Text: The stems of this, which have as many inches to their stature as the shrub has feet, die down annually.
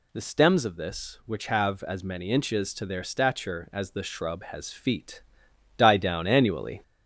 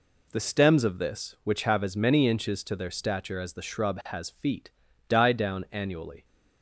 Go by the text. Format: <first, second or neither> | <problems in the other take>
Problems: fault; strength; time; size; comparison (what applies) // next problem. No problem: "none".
second | gets louder; slight; throughout; 2 dB